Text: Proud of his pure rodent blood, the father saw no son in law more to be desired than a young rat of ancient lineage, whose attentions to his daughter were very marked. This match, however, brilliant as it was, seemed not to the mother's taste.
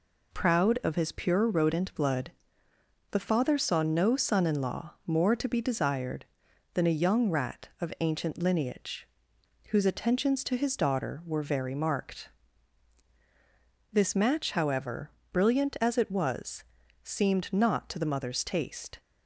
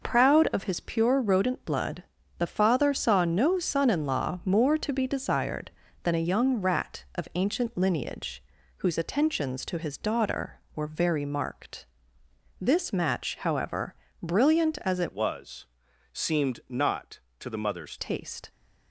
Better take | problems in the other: first | changes voice from "was" to "mother's"; from 15.1 to 17.9 s; 2.8 s long

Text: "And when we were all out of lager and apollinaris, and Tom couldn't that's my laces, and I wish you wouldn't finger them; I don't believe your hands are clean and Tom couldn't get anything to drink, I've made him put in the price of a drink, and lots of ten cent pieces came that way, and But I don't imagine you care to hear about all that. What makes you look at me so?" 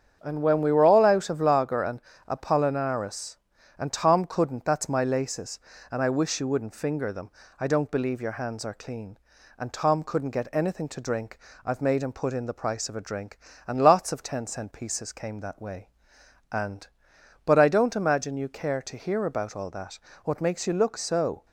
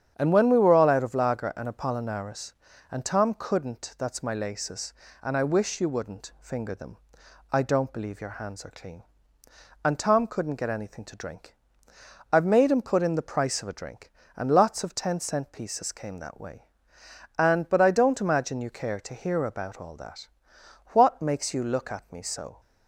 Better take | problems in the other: second | starts louder than the rest; strong; until 1.2 s; 8 dB; strong in the second // pauses between "and" and "apollinaris"; slight; at 2.0 s; 0.26 s long // skips "at me"; at 20.9 s

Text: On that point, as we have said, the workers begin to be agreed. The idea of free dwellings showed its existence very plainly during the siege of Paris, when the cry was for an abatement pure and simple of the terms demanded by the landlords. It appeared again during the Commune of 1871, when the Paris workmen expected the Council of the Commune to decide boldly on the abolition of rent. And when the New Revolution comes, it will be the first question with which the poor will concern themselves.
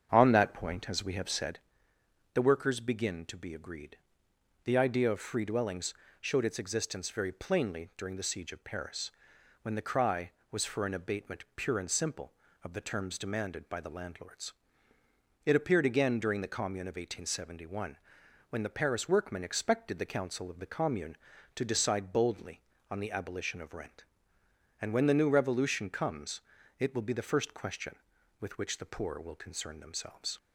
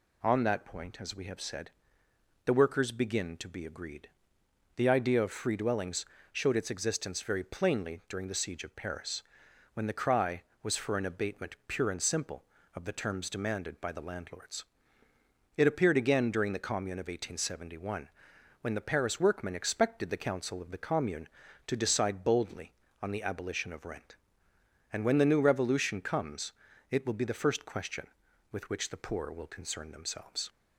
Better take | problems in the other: second | starts louder than the rest; strong; until 1.7 s; 7.5 dB // pauses between "dwellings" and "showed"; slight; at 5.9 s; 0.28 s long; slight in the second

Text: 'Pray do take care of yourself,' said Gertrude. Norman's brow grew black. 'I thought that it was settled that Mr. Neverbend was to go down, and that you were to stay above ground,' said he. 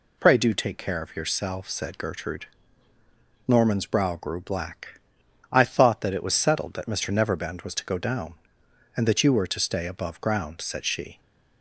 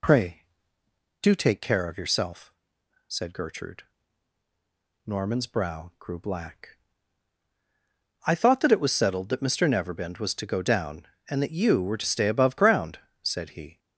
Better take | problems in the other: second | says "she" for "he"; at 10.8 s

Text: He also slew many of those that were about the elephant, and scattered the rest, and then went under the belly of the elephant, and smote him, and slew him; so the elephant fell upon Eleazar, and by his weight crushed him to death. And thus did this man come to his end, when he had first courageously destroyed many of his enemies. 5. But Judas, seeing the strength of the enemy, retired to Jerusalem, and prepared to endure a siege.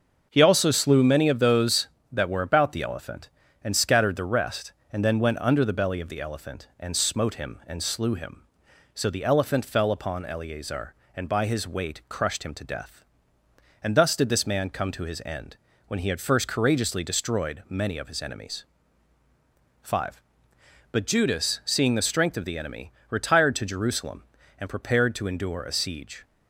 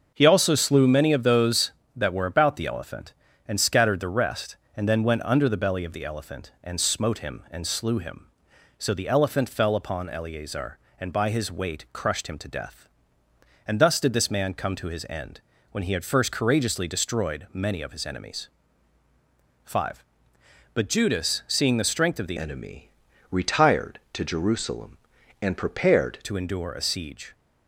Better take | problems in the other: first | starts louder than the rest; until 1.1 s; 6.5 dB; also in the first // changes voice from "enemy" to "prepared"; from 22.3 to 26.1 s; 3.8 s long

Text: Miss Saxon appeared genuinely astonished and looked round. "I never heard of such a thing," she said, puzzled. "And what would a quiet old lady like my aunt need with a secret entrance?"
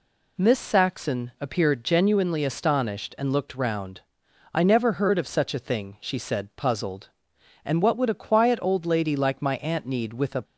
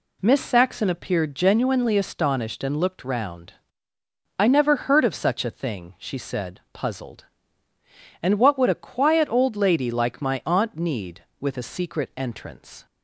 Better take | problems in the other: second | stops before "secret entrance"; at 10.4 s

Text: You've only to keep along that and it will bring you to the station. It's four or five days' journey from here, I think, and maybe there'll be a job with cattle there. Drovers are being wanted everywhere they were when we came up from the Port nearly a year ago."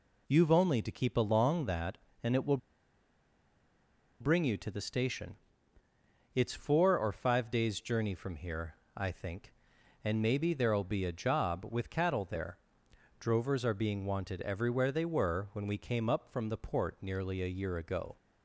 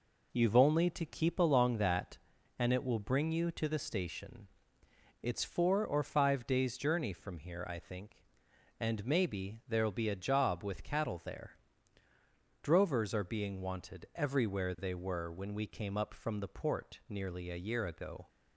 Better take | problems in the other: second | pauses between "will" and "bring"; strong; at 2.5 s; 1.6 s long

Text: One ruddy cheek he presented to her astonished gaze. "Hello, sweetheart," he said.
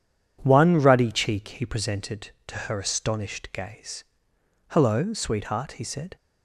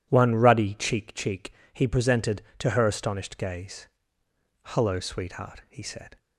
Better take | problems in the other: first | says "cheek" twice; at 1.1 s

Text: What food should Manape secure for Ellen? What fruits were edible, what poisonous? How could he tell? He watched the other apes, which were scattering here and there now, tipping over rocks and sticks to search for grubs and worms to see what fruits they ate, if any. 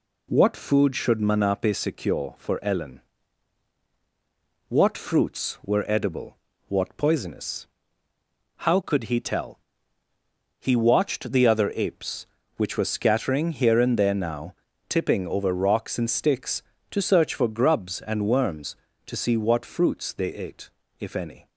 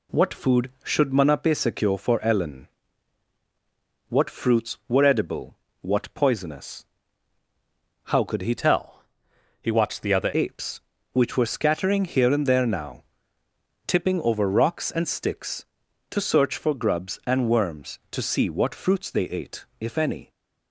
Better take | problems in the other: first | changes voice from "tell" to "other"; from 8.5 to 10.3 s; 1.8 s long

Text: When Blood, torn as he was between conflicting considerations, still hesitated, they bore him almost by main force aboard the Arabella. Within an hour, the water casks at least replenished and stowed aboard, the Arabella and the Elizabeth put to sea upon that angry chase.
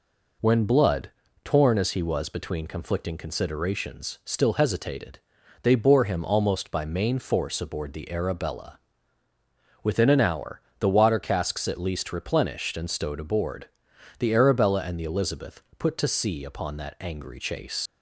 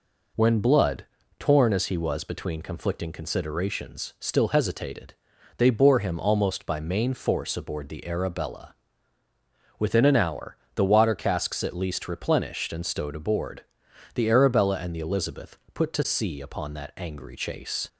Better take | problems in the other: second | pauses between "Elizabeth" and "put"; slight; at 15.6 s; 0.16 s long; slight in the second // leaves "chase" unfinished; at 17.8 s; 55 ms

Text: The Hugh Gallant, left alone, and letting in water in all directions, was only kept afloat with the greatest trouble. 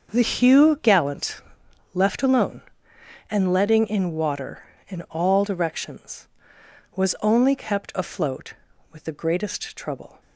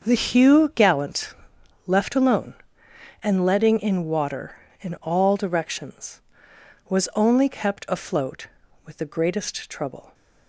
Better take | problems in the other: neither | starts louder than the rest; the same in both

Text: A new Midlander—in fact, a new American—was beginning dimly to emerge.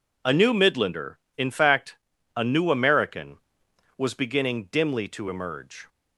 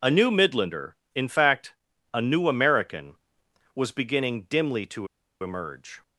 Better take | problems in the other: first | pauses between "to" and "emerge"; slight; at 5.0 s; 0.35 s long

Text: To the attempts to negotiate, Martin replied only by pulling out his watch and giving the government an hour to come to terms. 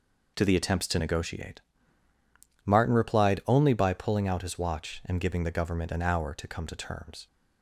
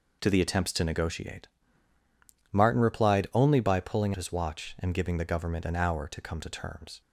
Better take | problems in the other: first | skips "out"; at 4.1 s

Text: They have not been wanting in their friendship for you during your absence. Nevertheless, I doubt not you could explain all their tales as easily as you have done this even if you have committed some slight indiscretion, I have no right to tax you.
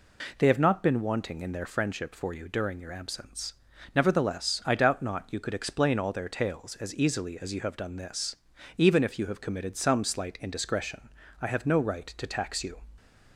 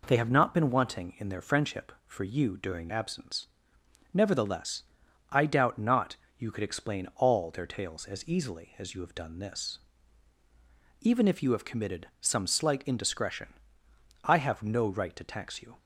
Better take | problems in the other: first | skips "your"; at 2.8 s // pauses between "not" and "you"; slight; at 6.1 s; 0.22 s long // pauses between "this" and "even"; at 9.7 s; 1.2 s long; also in the first

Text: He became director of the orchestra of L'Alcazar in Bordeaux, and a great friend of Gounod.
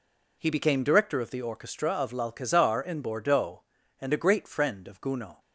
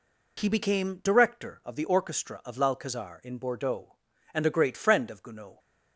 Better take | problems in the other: neither | none

